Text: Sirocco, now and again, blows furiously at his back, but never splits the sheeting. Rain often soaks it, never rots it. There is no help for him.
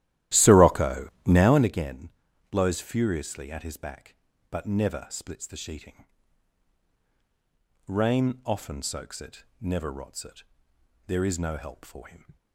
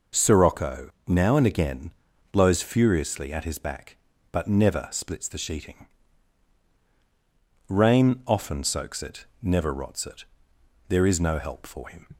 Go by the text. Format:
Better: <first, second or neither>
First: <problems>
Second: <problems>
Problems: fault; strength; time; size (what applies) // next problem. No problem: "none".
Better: second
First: starts louder than the rest; strong; until 1.7 s; 14 dB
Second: none